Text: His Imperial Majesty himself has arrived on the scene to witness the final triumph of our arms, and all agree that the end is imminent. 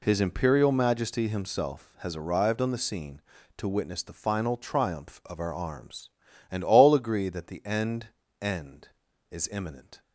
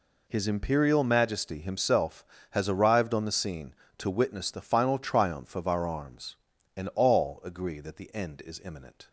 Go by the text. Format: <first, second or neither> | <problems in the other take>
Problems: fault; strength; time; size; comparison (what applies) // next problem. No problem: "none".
second | says "end" twice; at 8.4 s